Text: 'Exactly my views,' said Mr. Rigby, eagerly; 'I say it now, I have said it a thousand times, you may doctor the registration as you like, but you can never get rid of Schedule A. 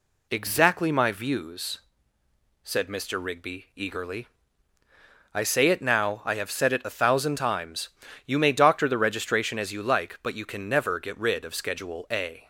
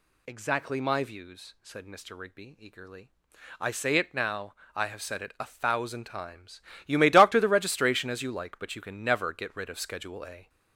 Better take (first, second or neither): first